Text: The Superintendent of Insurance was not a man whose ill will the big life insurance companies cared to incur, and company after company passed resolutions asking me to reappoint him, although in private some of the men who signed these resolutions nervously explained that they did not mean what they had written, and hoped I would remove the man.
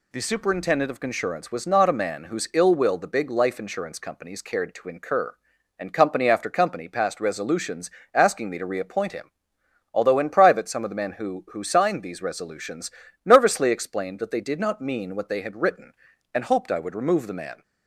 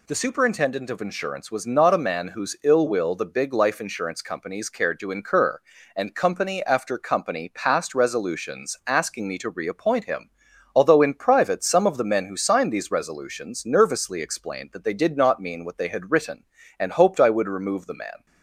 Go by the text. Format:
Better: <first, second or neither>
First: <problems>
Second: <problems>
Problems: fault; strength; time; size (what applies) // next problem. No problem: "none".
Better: second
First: pauses between "resolutions" and "asking"; slight; at 7.9 s; 0.22 s long // says "who" twice; at 11.5 s // pauses between "resolutions" and "nervously"; slight; at 12.9 s; 0.34 s long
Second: none